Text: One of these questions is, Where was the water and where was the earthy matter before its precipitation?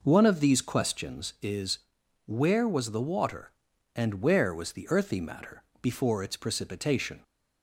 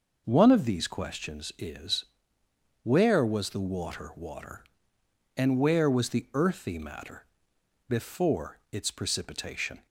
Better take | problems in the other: first | says "water" twice; at 4.1 s // pauses between "matter" and "before"; noticeable; at 7.2 s; 0.60 s long; slight in the first

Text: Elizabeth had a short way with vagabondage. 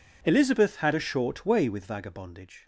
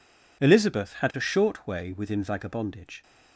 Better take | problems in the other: first | says "within" for "with"; at 1.9 s

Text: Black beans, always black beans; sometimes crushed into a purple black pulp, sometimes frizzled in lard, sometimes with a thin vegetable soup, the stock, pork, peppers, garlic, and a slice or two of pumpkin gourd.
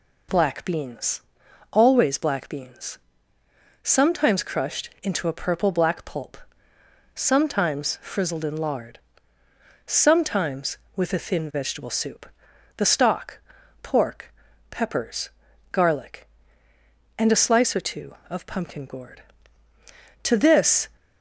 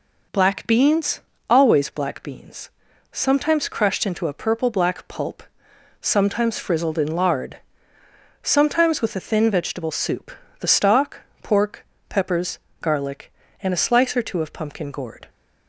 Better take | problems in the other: second | goes on to say "To this"; noticeable; from 20.2 s on; 0.66 s long

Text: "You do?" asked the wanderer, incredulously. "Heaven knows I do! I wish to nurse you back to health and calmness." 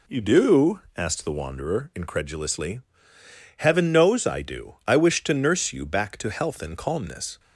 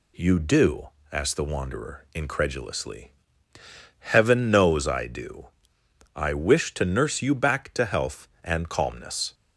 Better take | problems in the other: neither | none

